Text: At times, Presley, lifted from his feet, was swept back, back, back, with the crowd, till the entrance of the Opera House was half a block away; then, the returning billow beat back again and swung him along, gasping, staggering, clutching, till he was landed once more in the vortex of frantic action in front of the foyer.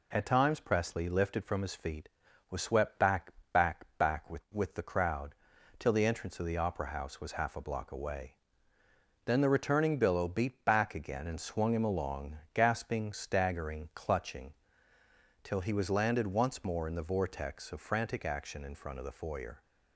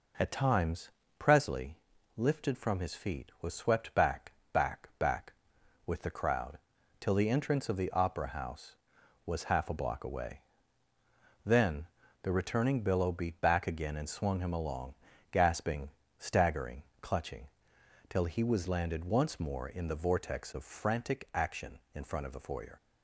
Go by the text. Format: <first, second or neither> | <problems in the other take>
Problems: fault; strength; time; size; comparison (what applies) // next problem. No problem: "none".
second | says "with" twice; at 4.5 s